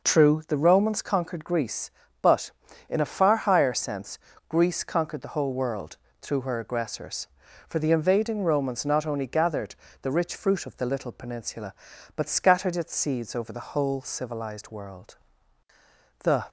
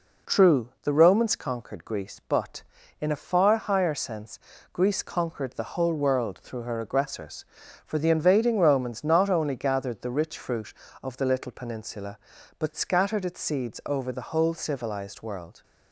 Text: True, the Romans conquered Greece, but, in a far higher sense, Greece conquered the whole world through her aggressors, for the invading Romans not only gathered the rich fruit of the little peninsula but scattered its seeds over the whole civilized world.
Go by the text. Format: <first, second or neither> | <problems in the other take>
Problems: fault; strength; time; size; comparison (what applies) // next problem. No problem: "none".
second | pauses between "world" and "through"; slight; at 5.9 s; 0.24 s long // pauses between "gathered" and "the"; slight; at 9.7 s; 0.28 s long // goes on to say "The"; slight; from 16.2 s on; 0.26 s long